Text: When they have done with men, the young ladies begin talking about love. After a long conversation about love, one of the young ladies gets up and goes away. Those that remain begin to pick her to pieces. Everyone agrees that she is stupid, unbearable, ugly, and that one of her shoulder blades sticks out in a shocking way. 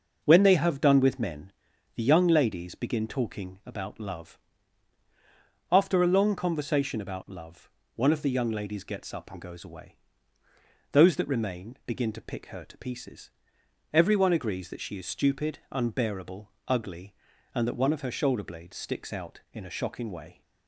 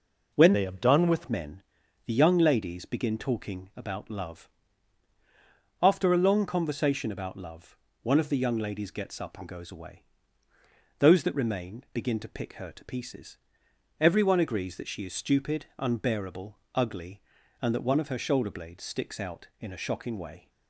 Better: first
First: none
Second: changes voice from "they" to "with"; from 0.5 to 1.2 s; 0.7 s long

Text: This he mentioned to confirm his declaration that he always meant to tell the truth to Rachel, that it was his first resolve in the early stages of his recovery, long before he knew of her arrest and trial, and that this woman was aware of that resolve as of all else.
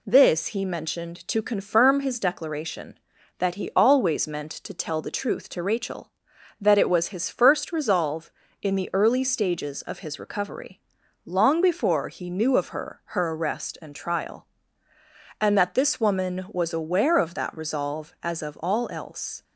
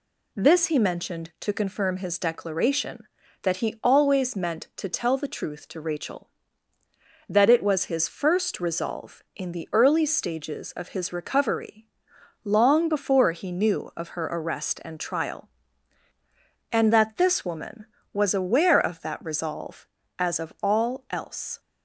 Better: second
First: says "her" twice; at 13.0 s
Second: none

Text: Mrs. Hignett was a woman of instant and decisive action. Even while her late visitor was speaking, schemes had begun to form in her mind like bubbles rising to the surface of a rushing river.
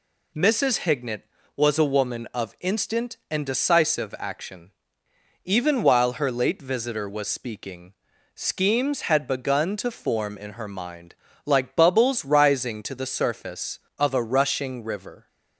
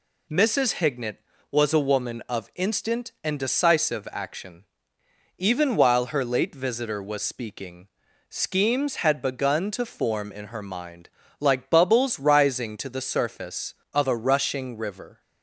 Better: neither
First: pauses between "mind" and "like"; slight; at 11.1 s; 0.28 s long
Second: pauses between "mind" and "like"; slight; at 11.0 s; 0.28 s long

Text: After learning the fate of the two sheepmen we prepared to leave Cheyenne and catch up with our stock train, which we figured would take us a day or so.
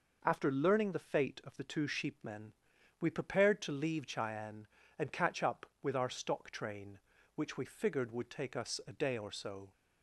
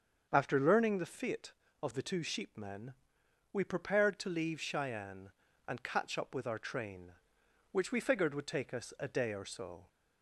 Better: first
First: pauses between "sheepmen" and "we"; noticeable; at 2.5 s; 0.46 s long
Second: starts louder than the rest; until 1.3 s; 7 dB // pauses between "sheepmen" and "we"; noticeable; at 2.9 s; 0.62 s long // skips "stock"; at 6.5 s

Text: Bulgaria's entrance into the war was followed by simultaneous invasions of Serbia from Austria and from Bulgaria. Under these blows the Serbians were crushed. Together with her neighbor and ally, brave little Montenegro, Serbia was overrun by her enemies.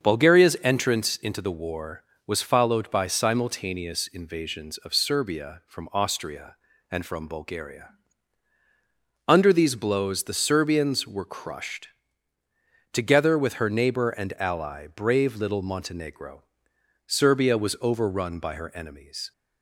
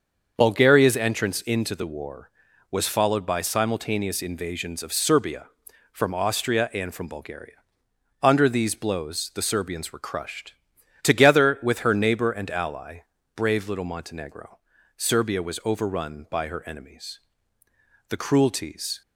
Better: first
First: starts louder than the rest; until 1.1 s; 7 dB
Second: starts louder than the rest; until 1.3 s; 6.5 dB // goes on to say "The cruelties"; noticeable; from 18.0 s on; 0.92 s long

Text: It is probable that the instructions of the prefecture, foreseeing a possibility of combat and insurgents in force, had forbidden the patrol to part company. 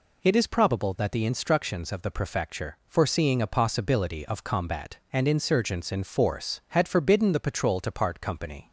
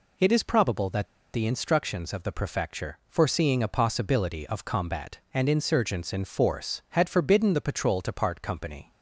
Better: first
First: none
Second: pauses between "that" and "the"; slight; at 1.0 s; 0.28 s long

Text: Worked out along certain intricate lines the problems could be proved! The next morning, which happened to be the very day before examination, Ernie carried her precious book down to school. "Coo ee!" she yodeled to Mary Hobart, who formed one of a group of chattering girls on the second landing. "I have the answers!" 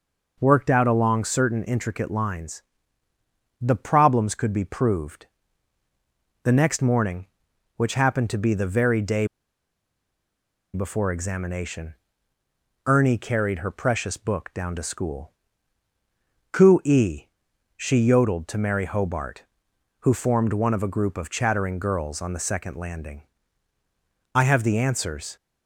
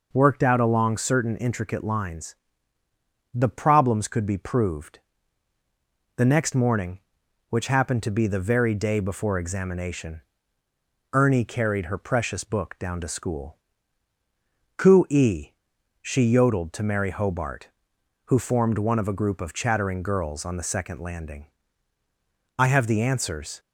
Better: second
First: pauses between "lines" and "the"; noticeable; at 2.6 s; 0.98 s long // pauses between "day" and "before"; strong; at 9.2 s; 1.4 s long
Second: pauses between "lines" and "the"; noticeable; at 2.3 s; 0.98 s long

